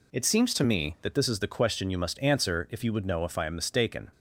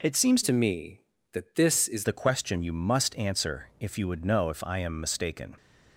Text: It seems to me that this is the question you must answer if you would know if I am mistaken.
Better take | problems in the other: first | changes voice from "to" to "is"; from 0.4 to 2.0 s; 1.6 s long

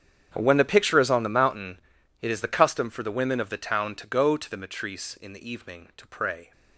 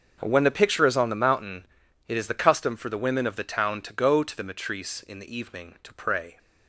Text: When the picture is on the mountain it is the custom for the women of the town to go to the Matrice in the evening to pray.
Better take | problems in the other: second | gets quieter; strong; throughout; 19.5 dB // starts louder than the rest; strong; until 1.3 s; 8.5 dB; also in the second // pauses between "mountain" and "it"; at 1.7 s; 0.44 s long; also in the second

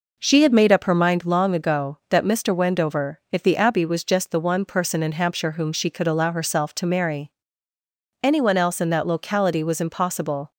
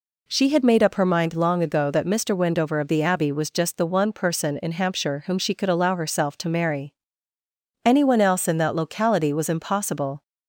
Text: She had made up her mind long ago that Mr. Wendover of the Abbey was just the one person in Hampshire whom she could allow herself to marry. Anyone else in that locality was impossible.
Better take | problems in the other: second | says "if" for "of"; at 3.3 s

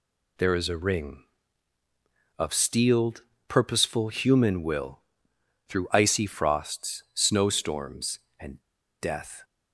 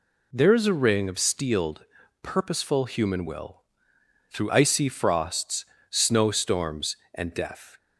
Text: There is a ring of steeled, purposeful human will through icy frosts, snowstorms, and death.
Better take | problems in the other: second | pauses between "will" and "through"; noticeable; at 4.9 s; 0.70 s long; noticeable in the second // pauses between "and" and "death"; at 8.6 s; 0.38 s long

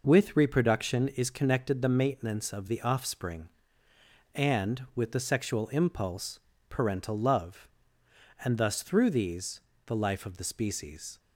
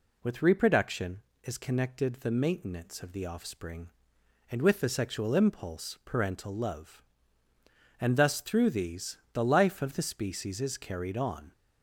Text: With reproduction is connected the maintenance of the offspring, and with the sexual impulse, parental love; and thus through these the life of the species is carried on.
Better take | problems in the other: second | pauses between "these" and "the"; slight; at 9.6 s; 0.26 s long; slight in the second // stops before "is carried on"; at 11.1 s

